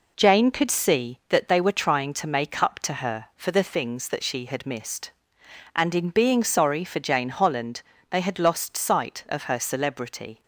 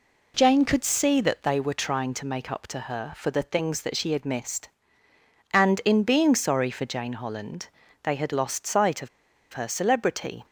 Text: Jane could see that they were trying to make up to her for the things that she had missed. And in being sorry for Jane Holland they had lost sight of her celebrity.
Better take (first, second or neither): first